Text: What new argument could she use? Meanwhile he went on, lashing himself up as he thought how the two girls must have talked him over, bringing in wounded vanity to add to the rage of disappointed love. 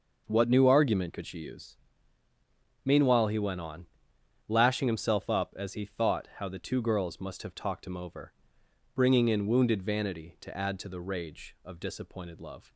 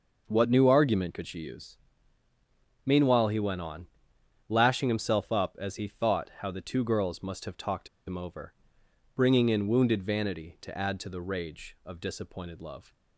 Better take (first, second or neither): first